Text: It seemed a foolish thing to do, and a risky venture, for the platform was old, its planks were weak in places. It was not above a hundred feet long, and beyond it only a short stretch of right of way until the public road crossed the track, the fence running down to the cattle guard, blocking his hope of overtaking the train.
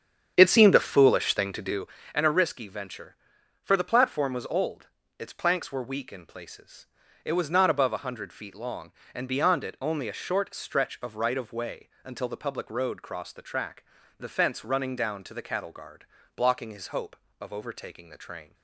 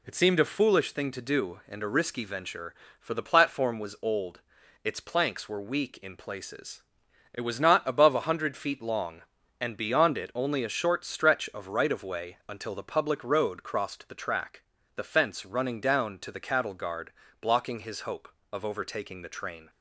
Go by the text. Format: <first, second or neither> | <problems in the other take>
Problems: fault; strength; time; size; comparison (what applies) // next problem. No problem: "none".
second | starts louder than the rest; strong; until 1.9 s; 8 dB